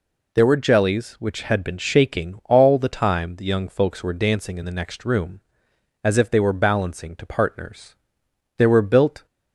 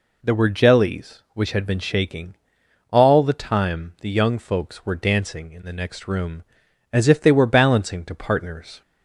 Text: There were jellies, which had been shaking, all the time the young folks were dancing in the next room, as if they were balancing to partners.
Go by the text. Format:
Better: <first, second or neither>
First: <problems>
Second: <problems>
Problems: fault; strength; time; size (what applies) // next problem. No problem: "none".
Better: second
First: goes on to say "There were built"; noticeable; from 8.5 s on; 0.68 s long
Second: none